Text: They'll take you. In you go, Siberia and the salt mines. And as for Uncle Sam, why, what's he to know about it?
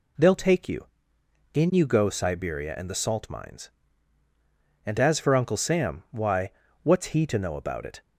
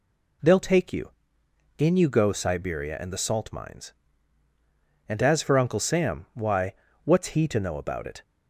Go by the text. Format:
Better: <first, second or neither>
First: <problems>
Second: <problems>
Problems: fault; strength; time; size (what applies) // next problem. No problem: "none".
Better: neither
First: none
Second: none